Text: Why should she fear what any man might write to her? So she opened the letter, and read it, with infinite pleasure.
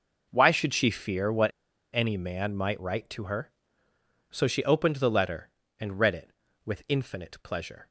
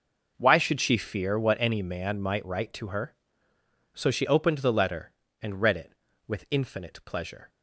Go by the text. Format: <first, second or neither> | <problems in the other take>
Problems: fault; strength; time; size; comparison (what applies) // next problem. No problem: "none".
second | pauses between "what" and "any"; at 1.4 s; 0.45 s long